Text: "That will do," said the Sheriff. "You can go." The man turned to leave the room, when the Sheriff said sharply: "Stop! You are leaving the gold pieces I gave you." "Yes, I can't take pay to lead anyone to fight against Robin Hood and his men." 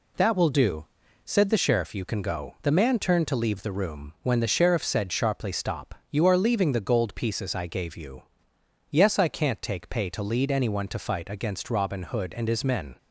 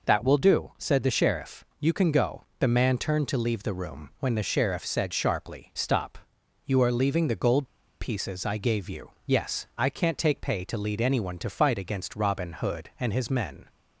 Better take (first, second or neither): first